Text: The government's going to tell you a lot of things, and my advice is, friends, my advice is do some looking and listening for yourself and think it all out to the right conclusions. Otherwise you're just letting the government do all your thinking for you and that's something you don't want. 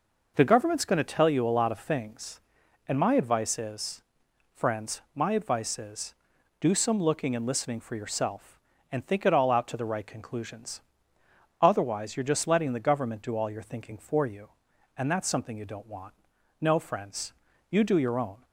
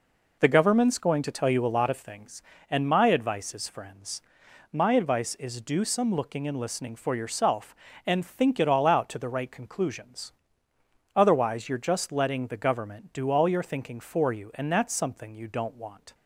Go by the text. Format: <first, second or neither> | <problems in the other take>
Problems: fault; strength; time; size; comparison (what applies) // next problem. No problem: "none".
second | goes on to say "No friends you do your own"; strong; from 16.5 s on; 1.8 s long